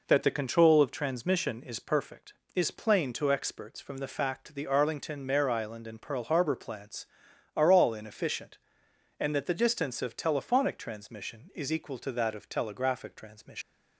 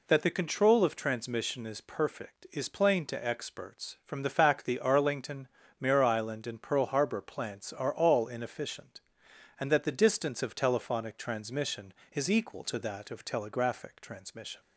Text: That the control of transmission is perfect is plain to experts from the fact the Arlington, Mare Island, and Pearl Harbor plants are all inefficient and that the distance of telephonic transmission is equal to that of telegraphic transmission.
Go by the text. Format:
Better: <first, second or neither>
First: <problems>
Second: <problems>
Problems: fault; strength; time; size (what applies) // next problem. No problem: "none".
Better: second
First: leaves "transmission" unfinished; at 13.6 s; 125 ms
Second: none